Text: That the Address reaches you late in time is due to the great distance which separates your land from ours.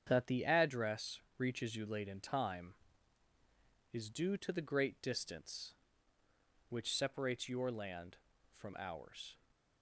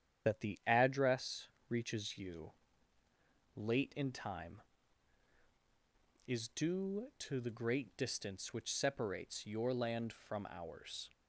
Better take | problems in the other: first | loses the start of "That"; at 0.2 s; 50 ms // starts louder than the rest; strong; until 1.3 s; 9.5 dB; strong in the first // pauses between "Address" and "reaches"; slight; at 1.4 s; 0.24 s long; slight in the first // pauses between "you" and "late"; at 2.5 s; 1.0 s long

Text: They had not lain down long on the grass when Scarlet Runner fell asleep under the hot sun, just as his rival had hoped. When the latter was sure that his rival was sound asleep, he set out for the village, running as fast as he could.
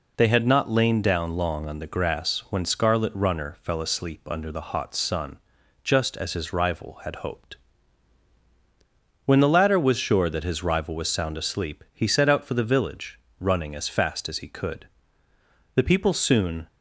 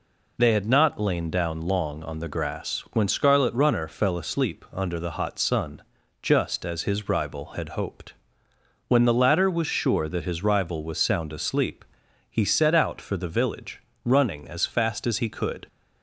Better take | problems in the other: second | goes on to say "The people soon"; noticeable; from 15.7 s on; 0.92 s long

